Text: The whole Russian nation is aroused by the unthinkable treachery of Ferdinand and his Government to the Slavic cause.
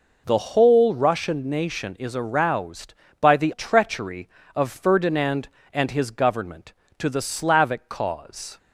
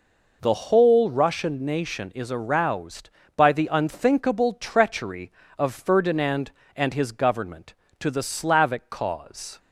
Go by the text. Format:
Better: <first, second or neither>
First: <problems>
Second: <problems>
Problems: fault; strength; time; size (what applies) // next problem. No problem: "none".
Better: second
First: skips "unthinkable"; at 3.5 s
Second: none